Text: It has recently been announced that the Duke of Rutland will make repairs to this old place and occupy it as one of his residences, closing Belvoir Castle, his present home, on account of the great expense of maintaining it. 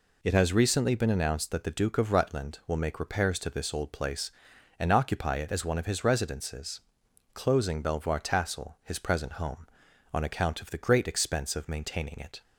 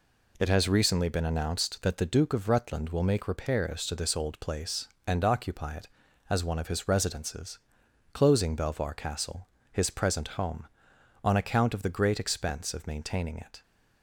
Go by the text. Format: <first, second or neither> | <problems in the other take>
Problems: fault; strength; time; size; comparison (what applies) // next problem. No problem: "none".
second | says "Tassel" for "Castle"; at 8.1 s